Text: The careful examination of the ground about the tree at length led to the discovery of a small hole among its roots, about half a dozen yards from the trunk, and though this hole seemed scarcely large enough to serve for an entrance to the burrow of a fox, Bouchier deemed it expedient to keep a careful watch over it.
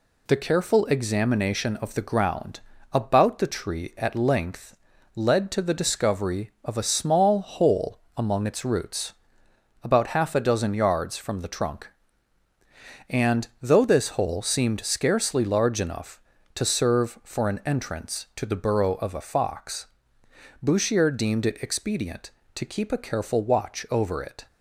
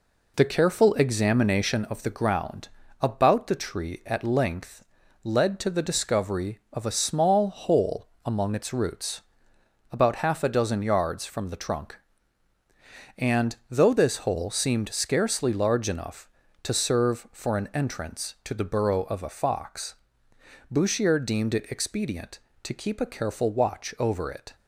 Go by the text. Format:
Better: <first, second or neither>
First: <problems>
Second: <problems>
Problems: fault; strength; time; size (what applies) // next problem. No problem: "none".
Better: first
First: pauses between "ground" and "about"; slight; at 2.5 s; 0.32 s long // pauses between "length" and "led"; at 4.7 s; 0.40 s long // pauses between "hole" and "among"; slight; at 8.0 s; 0.16 s long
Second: starts louder than the rest; until 1.9 s; 3.5 dB // pauses between "ground" and "about"; slight; at 2.6 s; 0.32 s long // pauses between "length" and "led"; at 4.8 s; 0.40 s long // pauses between "hole" and "among"; slight; at 8.0 s; 0.16 s long